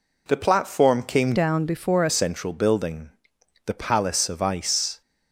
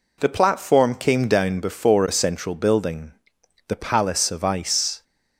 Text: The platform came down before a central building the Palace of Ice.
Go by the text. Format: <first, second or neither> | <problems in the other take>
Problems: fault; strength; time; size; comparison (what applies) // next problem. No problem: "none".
second | changes voice from "down" to "a"; from 1.3 to 2.1 s; 0.8 s long // pauses between "building" and "the"; noticeable; at 3.1 s; 0.56 s long; noticeable in the second